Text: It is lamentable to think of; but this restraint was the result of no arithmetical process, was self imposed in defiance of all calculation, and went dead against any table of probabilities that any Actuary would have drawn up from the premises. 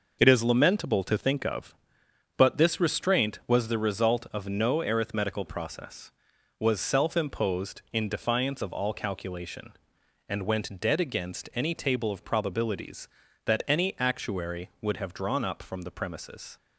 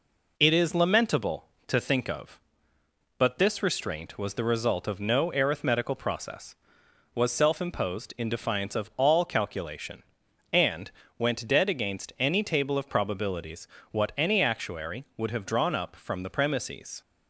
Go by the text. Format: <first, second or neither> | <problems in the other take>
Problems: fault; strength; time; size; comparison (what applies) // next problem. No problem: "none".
first | pauses between "and" and "went"; slight; at 10.9 s; 0.26 s long // says "what" for "that"; at 13.9 s